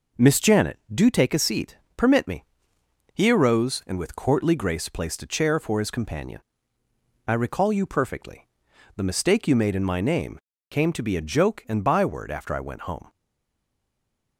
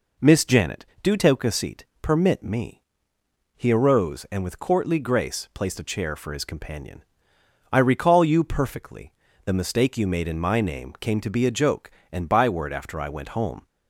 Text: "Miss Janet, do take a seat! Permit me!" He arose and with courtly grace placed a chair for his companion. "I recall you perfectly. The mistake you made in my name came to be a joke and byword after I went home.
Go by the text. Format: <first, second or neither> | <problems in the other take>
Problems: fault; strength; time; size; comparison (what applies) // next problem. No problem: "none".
second | pauses between "name" and "came"; slight; at 10.3 s; 0.30 s long // stays silent after the last word; noticeable; from 13.0 s on; 1.3 s long